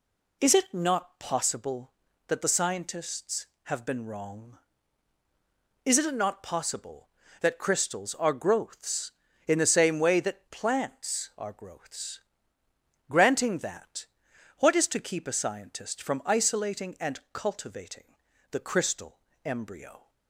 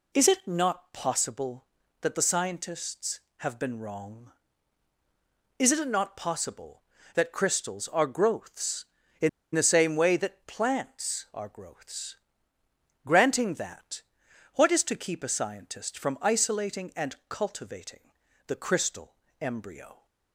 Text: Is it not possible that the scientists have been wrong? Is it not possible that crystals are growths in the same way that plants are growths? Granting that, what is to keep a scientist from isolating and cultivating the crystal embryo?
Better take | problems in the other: first | pauses between "in" and "the"; slight; at 9.2 s; 0.25 s long // pauses between "cultivating" and "the"; slight; at 18.1 s; 0.36 s long; slight in the first // pauses between "crystal" and "embryo"; slight; at 19.1 s; 0.26 s long; slight in the first

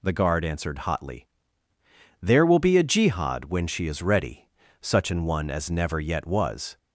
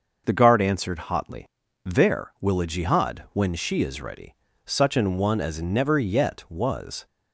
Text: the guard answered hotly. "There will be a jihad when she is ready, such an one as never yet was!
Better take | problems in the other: first | starts louder than the rest; noticeable; until 1.2 s; 6 dB // skips "be"; at 2.6 s

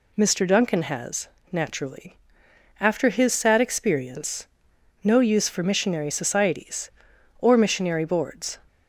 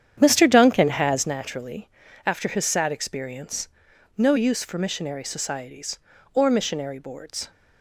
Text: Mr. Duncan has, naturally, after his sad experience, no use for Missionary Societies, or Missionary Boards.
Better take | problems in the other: first | starts louder than the rest; strong; until 1.4 s; 9 dB

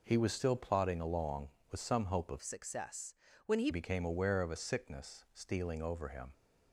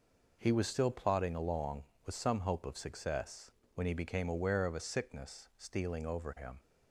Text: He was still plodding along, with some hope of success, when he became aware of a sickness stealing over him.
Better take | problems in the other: second | changes voice from "success" to "he"; from 2.4 to 3.6 s; 1.2 s long

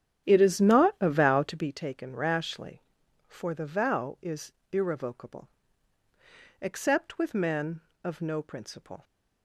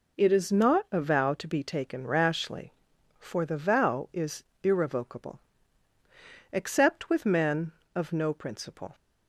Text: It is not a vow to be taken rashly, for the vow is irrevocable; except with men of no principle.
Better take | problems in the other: second | starts louder than the rest; strong; until 1.7 s; 9.5 dB // pauses between "is" and "irrevocable"; slight; at 4.5 s; 0.18 s long; slight in the second

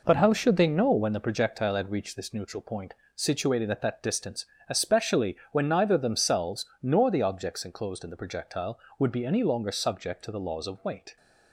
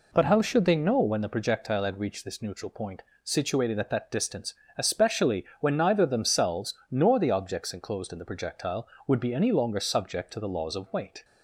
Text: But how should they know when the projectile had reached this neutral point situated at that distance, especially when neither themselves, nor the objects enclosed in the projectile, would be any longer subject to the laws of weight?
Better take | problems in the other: second | gets quieter; strong; throughout; 7.5 dB // pauses between "point" and "situated"; slight; at 2.9 s; 0.22 s long; slight in the second // pauses between "especially" and "when"; slight; at 5.3 s; 0.16 s long; slight in the second

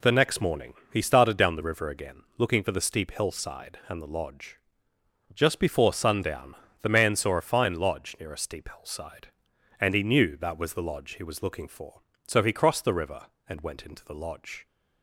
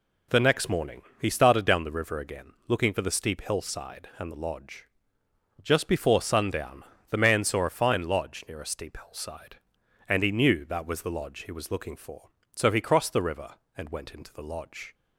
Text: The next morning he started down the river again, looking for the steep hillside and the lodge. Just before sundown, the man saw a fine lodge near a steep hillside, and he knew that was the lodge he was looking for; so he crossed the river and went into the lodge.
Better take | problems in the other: neither | pauses between "morning" and "he"; slight; the same in both

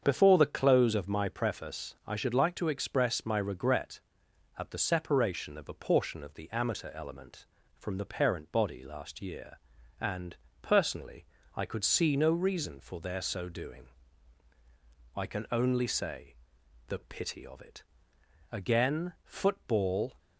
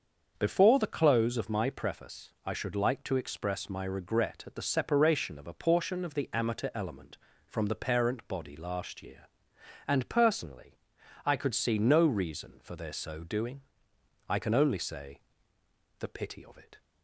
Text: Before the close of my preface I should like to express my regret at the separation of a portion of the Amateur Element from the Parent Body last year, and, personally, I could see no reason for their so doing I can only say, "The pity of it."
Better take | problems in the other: second | starts louder than the rest; strong; until 1.0 s; 7 dB; also in the second // pauses between "doing" and "I"; strong; at 13.8 s; 1.2 s long; noticeable in the second // goes on to say "Again football"; from 18.5 s on; 1.6 s long

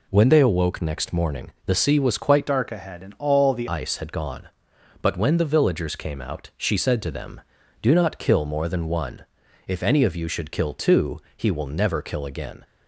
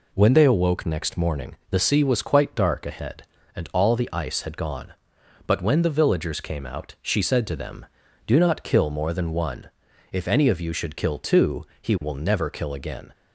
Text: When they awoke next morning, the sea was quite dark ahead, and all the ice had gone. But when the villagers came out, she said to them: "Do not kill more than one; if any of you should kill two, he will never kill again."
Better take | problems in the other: second | changes voice from "dark" to "the"; from 2.4 to 3.6 s; 1.2 s long

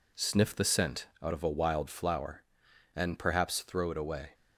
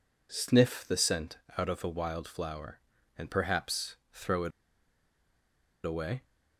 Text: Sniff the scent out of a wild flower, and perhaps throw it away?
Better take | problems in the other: first | pauses between "scent" and "out"; slight; at 1.3 s; 0.20 s long; slight in the first // pauses between "perhaps" and "throw"; slight; at 3.9 s; 0.16 s long // pauses between "it" and "away"; strong; at 4.5 s; 1.3 s long

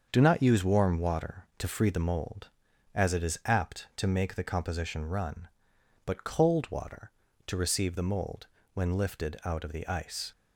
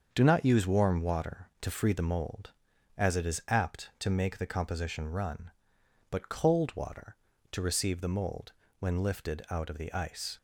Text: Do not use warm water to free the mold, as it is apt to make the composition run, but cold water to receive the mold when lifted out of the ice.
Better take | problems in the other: neither | starts louder than the rest; the same in both // pauses between "mold" and "when"; slight; the same in both

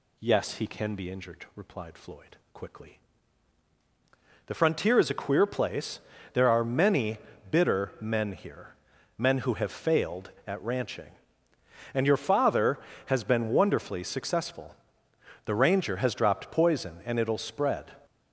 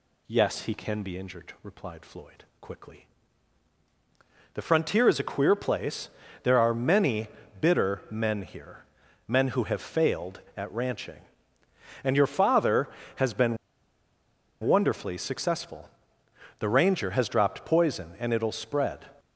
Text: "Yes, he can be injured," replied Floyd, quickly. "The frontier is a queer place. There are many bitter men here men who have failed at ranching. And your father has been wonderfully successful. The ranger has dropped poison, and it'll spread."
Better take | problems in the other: first | pauses between "many" and "bitter"; slight; at 7.2 s; 0.34 s long; slight in the first // pauses between "here" and "men"; noticeable; at 8.8 s; 0.46 s long; noticeable in the first // pauses between "been" and "wonderfully"; at 13.5 s; 1.0 s long

